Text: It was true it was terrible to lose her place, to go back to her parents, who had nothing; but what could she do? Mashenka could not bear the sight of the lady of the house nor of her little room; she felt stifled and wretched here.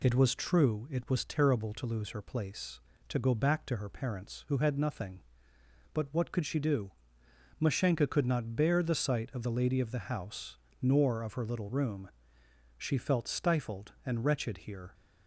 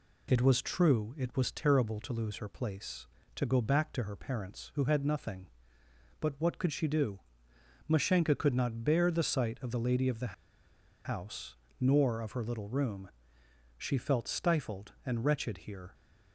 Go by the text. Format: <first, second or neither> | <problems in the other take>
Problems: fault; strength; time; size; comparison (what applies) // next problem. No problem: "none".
first | pauses between "the" and "house"; noticeable; at 10.3 s; 0.72 s long // pauses between "house" and "nor"; slight; at 11.5 s; 0.24 s long; slight in the first